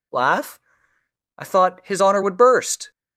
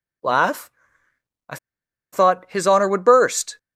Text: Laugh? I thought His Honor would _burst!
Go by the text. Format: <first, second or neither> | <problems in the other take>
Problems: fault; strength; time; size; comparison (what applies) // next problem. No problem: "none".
first | pauses between "I" and "thought"; noticeable; at 1.5 s; 0.56 s long